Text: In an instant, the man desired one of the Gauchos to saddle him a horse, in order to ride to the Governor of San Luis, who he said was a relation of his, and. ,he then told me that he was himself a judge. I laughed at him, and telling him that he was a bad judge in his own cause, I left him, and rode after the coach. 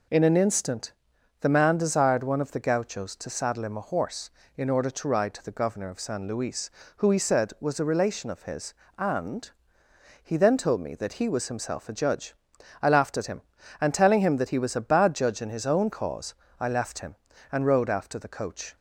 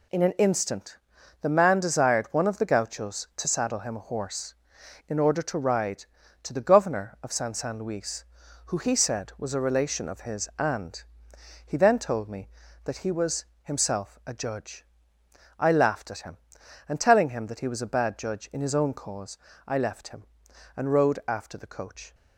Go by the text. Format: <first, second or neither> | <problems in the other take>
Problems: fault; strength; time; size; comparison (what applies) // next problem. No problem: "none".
first | says "San" twice; at 7.5 s // pauses between "was" and "himself"; slight; at 13.4 s; 0.18 s long